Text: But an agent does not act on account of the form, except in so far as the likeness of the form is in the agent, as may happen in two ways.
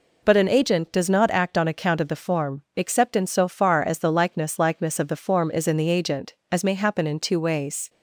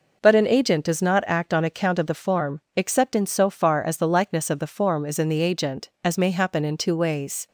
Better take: second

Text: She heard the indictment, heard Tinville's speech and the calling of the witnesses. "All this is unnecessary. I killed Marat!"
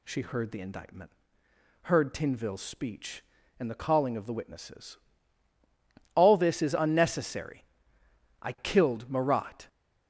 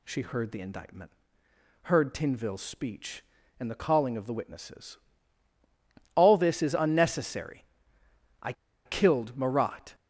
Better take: first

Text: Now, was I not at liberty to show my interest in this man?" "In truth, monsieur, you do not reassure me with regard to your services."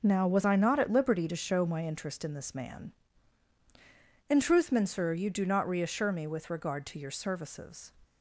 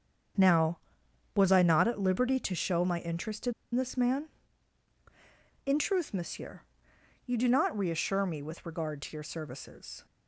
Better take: first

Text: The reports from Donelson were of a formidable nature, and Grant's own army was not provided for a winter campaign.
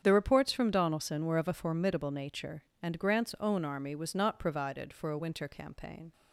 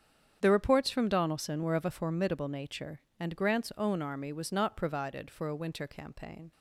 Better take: neither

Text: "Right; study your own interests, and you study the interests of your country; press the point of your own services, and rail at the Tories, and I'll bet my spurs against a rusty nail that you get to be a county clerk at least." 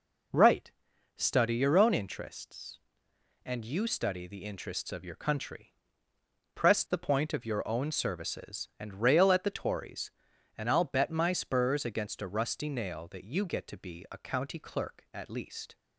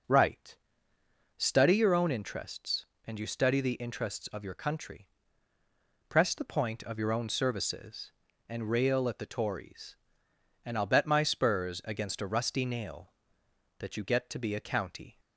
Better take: first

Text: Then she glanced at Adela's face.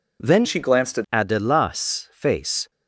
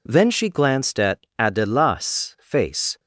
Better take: second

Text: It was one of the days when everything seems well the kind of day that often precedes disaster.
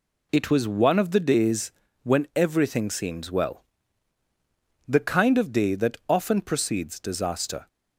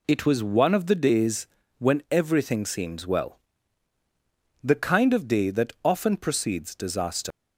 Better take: first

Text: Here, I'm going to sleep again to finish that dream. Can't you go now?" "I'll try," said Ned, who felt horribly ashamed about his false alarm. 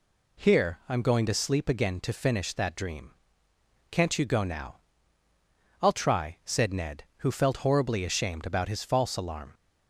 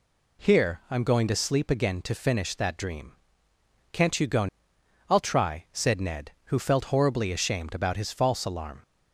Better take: first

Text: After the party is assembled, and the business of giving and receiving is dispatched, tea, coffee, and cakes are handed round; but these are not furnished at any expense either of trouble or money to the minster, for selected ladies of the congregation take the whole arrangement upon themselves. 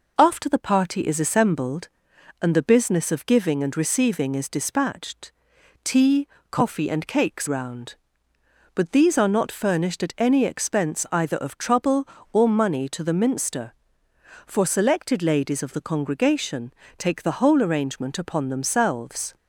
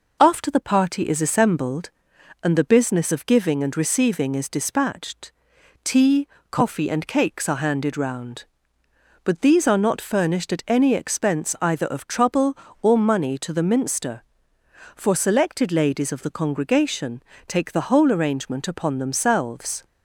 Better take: second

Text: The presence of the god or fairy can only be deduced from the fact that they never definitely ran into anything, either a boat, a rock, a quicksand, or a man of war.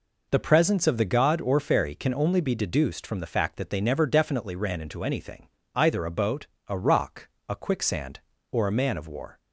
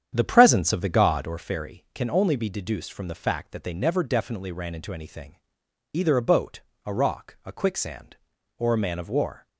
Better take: first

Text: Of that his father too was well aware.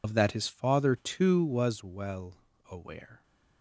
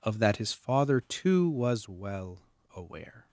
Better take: second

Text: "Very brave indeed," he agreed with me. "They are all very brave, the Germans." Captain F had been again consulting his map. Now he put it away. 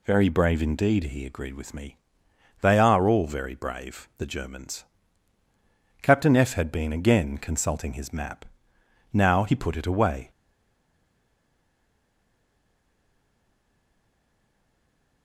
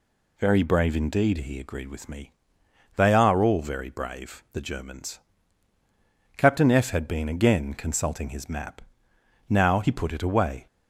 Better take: second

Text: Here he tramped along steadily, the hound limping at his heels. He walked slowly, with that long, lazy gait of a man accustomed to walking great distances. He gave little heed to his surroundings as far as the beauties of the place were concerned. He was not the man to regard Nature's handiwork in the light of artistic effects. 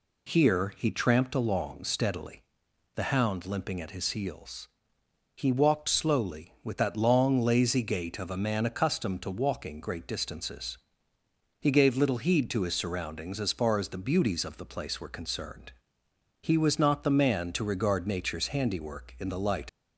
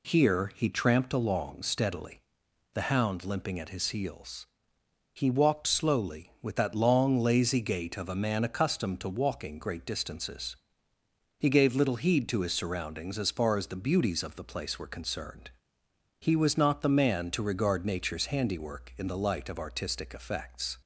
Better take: second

